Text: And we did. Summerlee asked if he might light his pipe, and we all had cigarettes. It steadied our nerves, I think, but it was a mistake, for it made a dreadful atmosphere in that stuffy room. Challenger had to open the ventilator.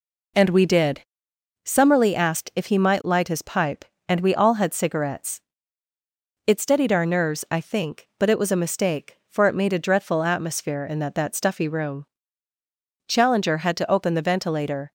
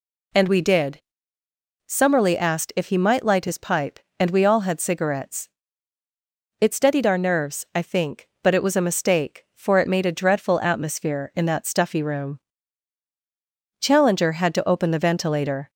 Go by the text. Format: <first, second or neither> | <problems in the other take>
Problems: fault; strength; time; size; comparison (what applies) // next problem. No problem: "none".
second | says "that" twice; at 11.1 s